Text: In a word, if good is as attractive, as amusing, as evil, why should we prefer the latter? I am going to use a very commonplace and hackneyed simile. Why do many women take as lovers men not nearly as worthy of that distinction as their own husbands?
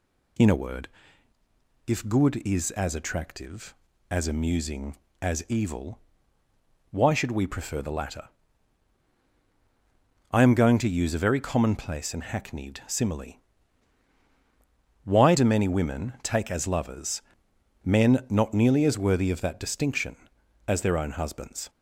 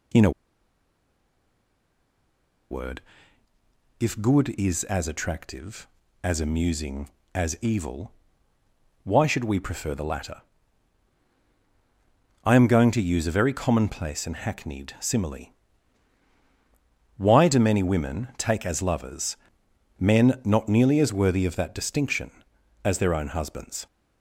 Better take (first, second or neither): first